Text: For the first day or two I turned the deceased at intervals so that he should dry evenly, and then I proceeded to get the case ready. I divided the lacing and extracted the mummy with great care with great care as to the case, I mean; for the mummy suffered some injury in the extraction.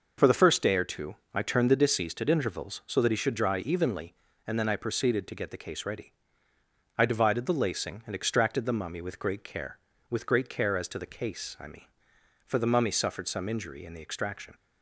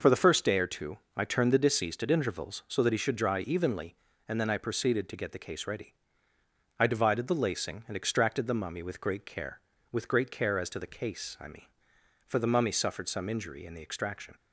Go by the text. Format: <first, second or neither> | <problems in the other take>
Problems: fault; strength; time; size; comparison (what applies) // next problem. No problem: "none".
neither | pauses between "two" and "I"; slight; the same in both